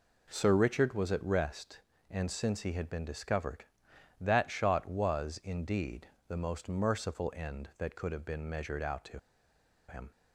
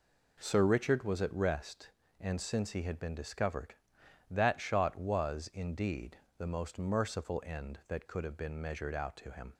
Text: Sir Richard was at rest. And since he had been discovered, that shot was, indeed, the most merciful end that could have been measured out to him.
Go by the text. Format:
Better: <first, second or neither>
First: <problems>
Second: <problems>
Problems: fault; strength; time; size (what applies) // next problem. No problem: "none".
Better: second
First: pauses between "to" and "him"; noticeable; at 9.1 s; 0.69 s long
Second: none